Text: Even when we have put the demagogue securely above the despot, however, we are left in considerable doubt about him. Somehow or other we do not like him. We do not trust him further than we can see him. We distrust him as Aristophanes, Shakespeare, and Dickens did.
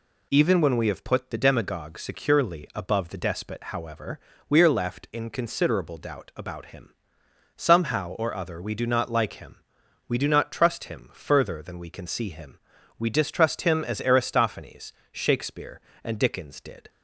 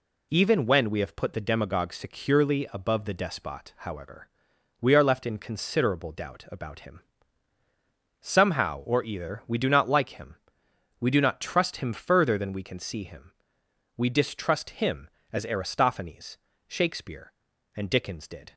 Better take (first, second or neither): first